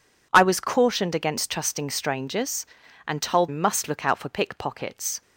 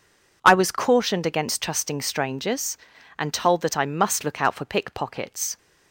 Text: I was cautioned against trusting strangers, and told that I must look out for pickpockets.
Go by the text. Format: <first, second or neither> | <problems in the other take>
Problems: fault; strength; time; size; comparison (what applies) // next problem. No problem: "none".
second | skips "that I"; at 3.4 s